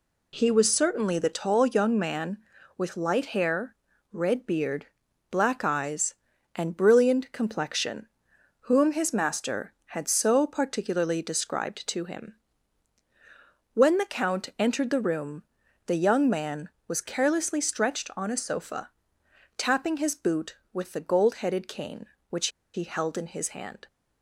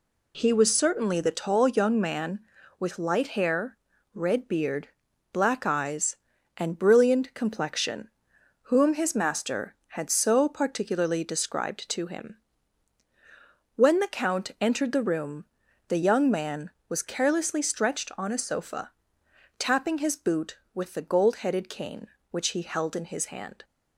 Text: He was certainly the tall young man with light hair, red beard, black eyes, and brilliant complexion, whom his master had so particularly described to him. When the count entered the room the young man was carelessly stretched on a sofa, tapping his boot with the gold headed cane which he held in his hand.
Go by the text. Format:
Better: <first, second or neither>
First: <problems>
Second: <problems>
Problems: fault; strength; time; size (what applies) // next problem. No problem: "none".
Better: second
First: pauses between "room" and "the"; at 15.4 s; 0.42 s long // pauses between "which" and "he"; slight; at 22.4 s; 0.25 s long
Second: pauses between "room" and "the"; at 15.4 s; 0.42 s long